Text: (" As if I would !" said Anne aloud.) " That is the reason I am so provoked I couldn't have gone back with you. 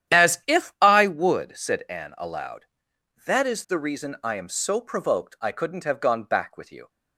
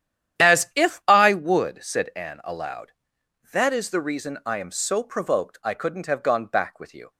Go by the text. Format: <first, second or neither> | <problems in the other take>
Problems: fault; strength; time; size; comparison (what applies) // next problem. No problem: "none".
neither | starts louder than the rest; strong; the same in both